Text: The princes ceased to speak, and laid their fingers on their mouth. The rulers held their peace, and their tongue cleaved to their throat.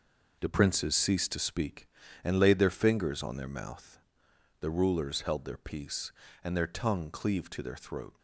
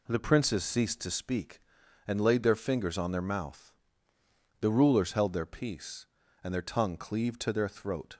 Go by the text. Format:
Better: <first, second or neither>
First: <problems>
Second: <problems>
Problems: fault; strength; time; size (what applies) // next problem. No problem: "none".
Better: second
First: gets quieter; strong; throughout; 8.5 dB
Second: none